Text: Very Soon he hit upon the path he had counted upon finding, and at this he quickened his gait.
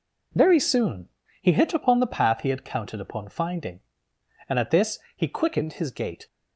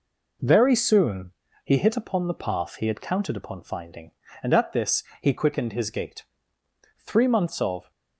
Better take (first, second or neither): first